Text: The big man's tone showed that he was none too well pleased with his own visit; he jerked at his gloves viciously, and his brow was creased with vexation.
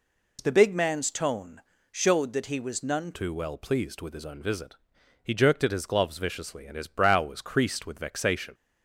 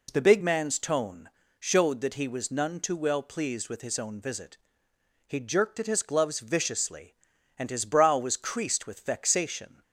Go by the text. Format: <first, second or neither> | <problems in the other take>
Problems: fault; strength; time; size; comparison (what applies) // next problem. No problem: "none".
second | pauses between "tone" and "showed"; slight; at 1.5 s; 0.32 s long; slight in the second // changes voice at "too"; from 3.1 s on; 5.4 s long